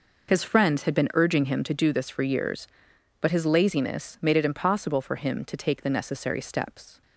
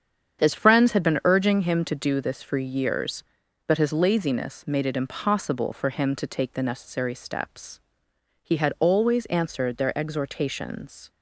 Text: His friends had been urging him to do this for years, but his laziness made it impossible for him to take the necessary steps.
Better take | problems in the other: first | starts louder than the rest; strong; until 1.4 s; 8 dB // goes on to say "He had always answered their exhortations"; strong; from 8.4 s on; 2.6 s long

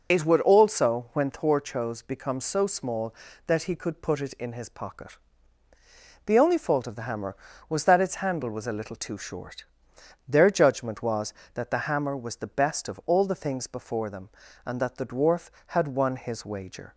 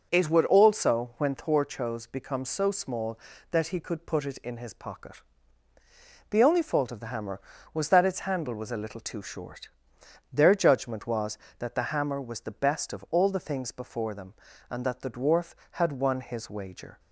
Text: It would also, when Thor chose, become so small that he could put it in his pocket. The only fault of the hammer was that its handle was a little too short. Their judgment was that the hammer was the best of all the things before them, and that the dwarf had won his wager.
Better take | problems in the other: second | loses the start of "It"; at 0.1 s; 35 ms

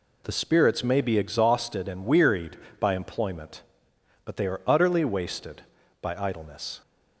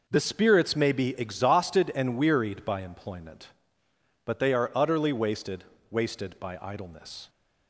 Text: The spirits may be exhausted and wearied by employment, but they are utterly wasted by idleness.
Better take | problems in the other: first | says "wasted" twice; at 5.8 s

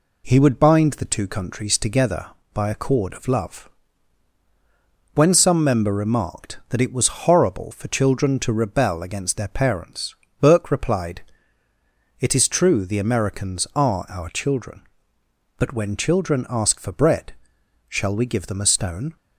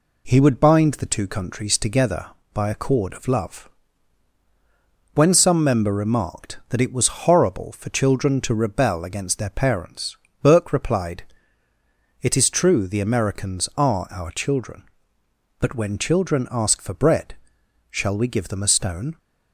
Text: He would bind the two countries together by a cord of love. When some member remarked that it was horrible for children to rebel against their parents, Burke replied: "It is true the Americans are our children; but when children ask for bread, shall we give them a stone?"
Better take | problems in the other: neither | none

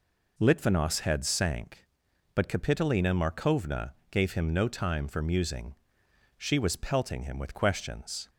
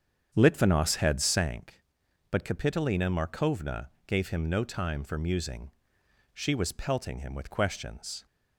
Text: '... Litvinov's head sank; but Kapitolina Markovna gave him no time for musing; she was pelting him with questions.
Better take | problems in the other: first | starts louder than the rest; strong; until 1.5 s; 8 dB // pauses between "Markovna" and "gave"; slight; at 3.8 s; 0.18 s long; slight in the first

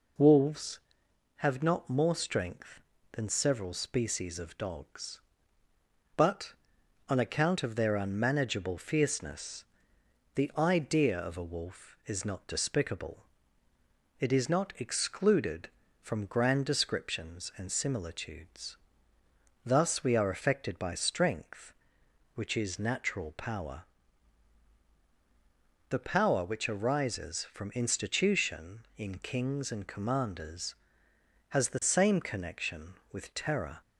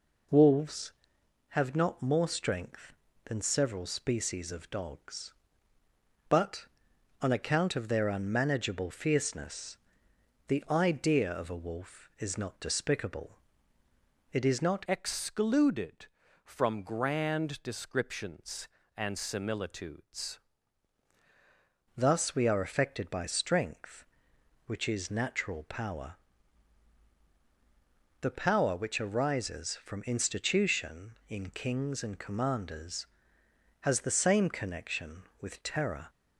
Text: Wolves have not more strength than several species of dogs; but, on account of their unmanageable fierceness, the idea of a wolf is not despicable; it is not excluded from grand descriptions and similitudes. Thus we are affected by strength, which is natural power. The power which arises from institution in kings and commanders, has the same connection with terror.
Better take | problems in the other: first | changes voice from "excluded" to "similitudes"; from 14.8 to 20.3 s; 5.5 s long

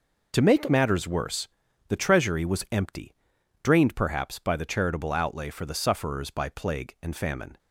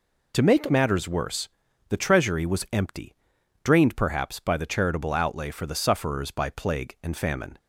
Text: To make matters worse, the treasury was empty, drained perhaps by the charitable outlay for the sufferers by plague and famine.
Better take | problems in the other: second | gets quieter; strong; throughout; 11 dB

